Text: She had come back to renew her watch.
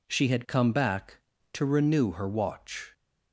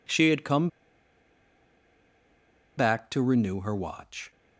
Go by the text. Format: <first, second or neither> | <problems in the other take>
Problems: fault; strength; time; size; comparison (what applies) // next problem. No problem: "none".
first | pauses between "come" and "back"; strong; at 0.6 s; 2.0 s long